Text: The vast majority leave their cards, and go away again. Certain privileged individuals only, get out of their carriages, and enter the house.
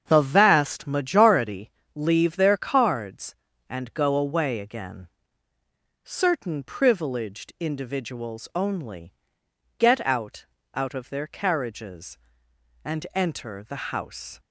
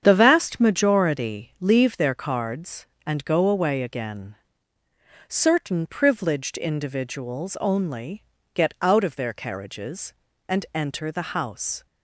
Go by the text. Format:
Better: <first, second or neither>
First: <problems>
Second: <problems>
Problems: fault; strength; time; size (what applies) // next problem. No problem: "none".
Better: second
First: starts louder than the rest; strong; until 1.0 s; 7.5 dB // pauses between "majority" and "leave"; slight; at 1.6 s; 0.24 s long // says "out" twice; at 10.7 s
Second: starts louder than the rest; strong; until 1.0 s; 8 dB